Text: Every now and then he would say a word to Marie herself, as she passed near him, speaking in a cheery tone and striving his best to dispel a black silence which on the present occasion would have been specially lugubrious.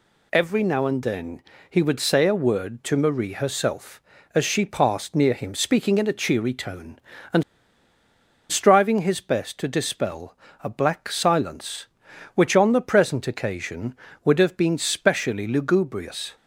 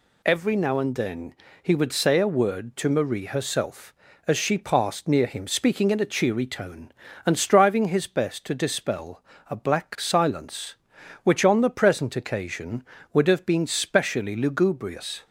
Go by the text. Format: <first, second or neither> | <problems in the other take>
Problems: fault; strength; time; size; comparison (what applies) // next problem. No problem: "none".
second | pauses between "then" and "he"; slight; at 1.4 s; 0.30 s long; slight in the second // pauses between "and" and "striving"; at 7.4 s; 1.0 s long // pauses between "dispel" and "a"; slight; at 10.3 s; 0.30 s long; slight in the second